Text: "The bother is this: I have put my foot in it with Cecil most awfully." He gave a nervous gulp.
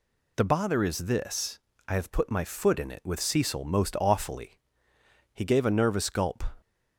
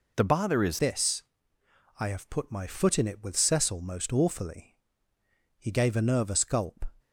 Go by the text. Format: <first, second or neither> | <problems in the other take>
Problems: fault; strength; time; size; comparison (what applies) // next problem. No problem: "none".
first | changes voice at "this"; from 0.7 s on; 6.1 s long